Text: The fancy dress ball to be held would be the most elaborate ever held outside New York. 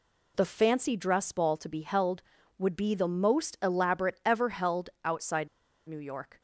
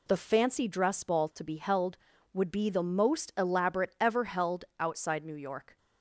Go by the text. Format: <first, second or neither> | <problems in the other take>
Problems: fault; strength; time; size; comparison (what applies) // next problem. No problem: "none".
second | pauses between "outside" and "New"; at 5.4 s; 0.40 s long